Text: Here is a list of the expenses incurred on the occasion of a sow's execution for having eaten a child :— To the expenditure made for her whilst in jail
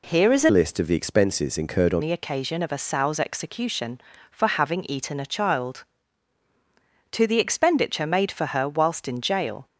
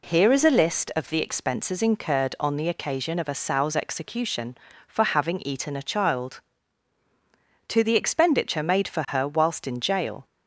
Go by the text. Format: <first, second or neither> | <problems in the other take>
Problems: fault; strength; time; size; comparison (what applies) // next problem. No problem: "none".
second | changes voice from "list" to "on"; from 0.5 to 2.0 s; 1.5 s long